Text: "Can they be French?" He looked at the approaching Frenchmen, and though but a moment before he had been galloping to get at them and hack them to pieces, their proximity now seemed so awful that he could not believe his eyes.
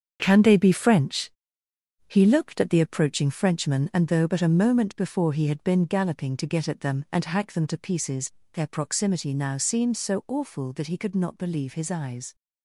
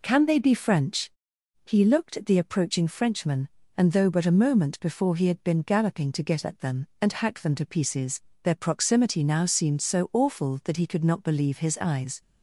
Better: second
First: gets quieter; strong; throughout; 8 dB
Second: none

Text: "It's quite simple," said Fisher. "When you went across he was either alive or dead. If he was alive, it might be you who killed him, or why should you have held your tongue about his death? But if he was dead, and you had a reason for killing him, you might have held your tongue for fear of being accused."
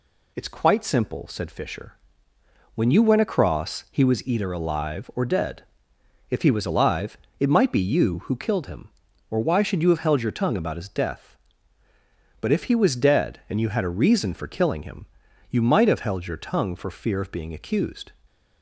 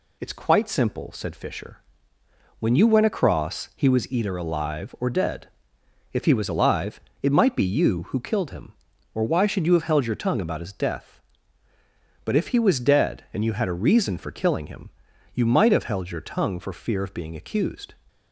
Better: neither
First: none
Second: none

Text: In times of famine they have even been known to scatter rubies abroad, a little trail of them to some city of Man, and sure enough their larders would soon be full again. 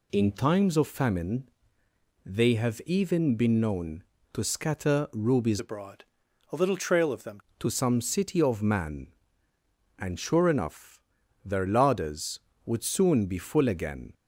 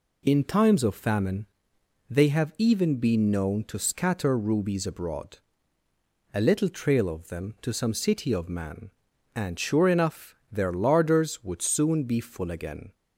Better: second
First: pauses between "famine" and "they"; noticeable; at 1.4 s; 0.78 s long // changes voice from "abroad" to "them"; from 5.5 to 7.3 s; 1.8 s long // pauses between "enough" and "their"; at 11.0 s; 0.42 s long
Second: pauses between "famine" and "they"; noticeable; at 1.4 s; 0.64 s long

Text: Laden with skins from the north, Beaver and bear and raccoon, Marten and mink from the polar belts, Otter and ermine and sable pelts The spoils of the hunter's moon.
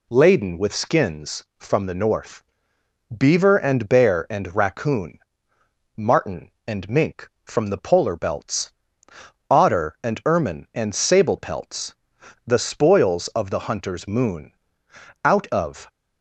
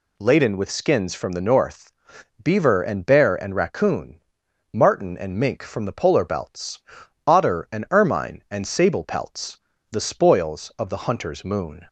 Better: second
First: pauses between "pelts" and "The"; noticeable; at 11.9 s; 0.52 s long // goes on to say "Out of"; noticeable; from 15.2 s on; 0.64 s long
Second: pauses between "pelts" and "The"; slight; at 9.5 s; 0.34 s long

